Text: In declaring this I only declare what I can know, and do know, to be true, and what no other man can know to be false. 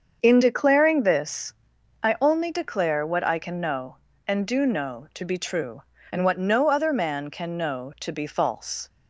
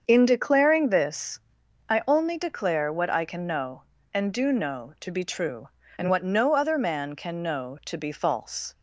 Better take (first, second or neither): neither